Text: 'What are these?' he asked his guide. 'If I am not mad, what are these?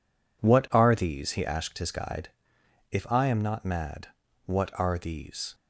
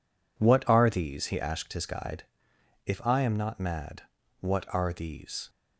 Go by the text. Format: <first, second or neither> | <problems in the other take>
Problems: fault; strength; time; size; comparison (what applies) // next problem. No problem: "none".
neither | none